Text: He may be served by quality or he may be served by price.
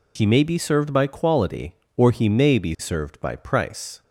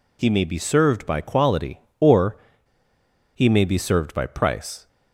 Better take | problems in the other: first | pauses between "or" and "he"; at 2.3 s; 0.98 s long

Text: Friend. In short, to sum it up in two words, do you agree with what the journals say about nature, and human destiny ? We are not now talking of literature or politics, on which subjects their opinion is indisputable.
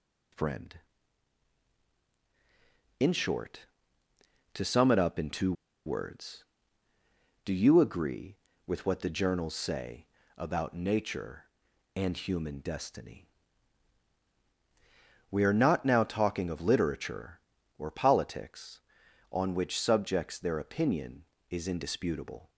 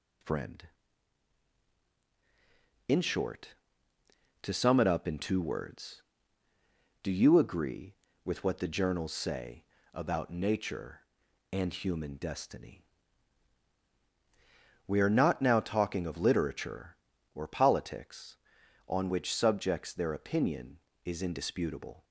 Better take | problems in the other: second | pauses between "two" and "words"; slight; at 5.5 s; 0.33 s long // pauses between "say" and "about"; slight; at 10.0 s; 0.30 s long; slight in the second

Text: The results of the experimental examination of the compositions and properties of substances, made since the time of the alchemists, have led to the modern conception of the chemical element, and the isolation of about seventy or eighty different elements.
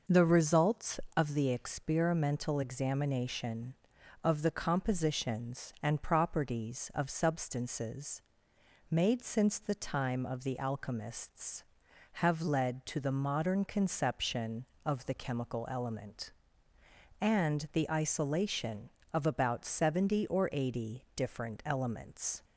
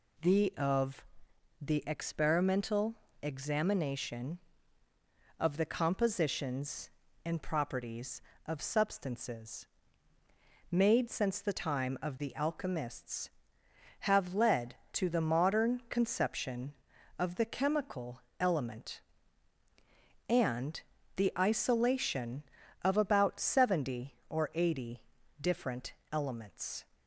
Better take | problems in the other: first | skips "results"; at 0.5 s // pauses between "of" and "the"; noticeable; at 1.0 s; 0.56 s long // pauses between "experimental" and "examination"; slight; at 2.9 s; 0.26 s long // pauses between "chemical" and "element"; slight; at 18.2 s; 0.20 s long // pauses between "and" and "the"; slight; at 20.8 s; 0.34 s long // pauses between "eighty" and "different"; at 25.0 s; 0.40 s long // pauses between "different" and "elements"; slight; at 25.9 s; 0.18 s long

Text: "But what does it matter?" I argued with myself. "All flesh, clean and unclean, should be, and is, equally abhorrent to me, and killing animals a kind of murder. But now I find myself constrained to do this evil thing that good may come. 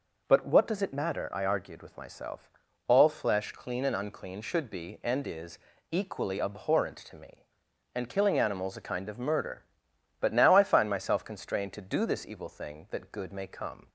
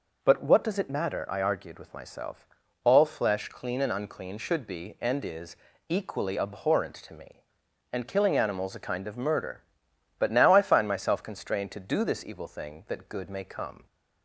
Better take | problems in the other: neither | none

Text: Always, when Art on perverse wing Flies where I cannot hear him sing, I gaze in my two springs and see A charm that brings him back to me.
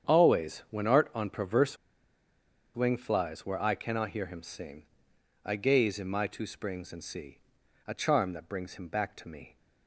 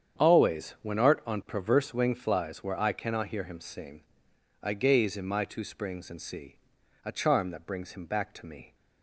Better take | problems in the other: second | starts louder than the rest; strong; until 1.2 s; 8 dB; strong in the second // pauses between "perverse" and "wing"; at 1.7 s; 1.0 s long // pauses between "see" and "A"; noticeable; at 7.3 s; 0.50 s long; noticeable in the second

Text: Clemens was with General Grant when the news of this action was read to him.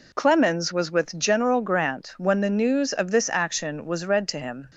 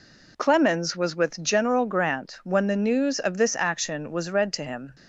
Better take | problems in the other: neither | none

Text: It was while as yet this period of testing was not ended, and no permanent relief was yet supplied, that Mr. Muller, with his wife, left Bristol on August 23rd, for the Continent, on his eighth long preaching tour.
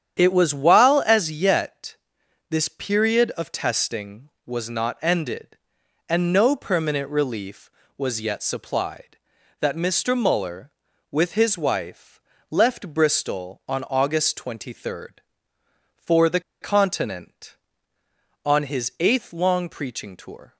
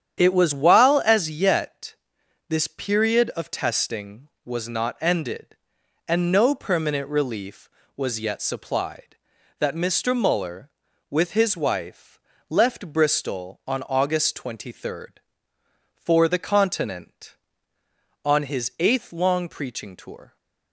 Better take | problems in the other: second | starts louder than the rest; strong; until 1.2 s; 9 dB; strong in the second // pauses between "yet" and "this"; noticeable; at 1.9 s; 0.56 s long; noticeable in the second // pauses between "the" and "Continent"; slight; at 16.3 s; 0.21 s long

